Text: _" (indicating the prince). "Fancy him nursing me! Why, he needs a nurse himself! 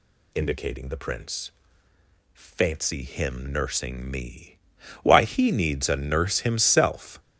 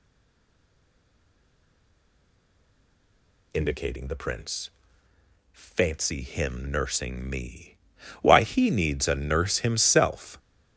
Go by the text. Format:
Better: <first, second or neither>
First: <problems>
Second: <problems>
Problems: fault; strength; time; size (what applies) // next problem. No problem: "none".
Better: first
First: none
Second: stays silent before the first word; strong; until 3.5 s; 3.5 s long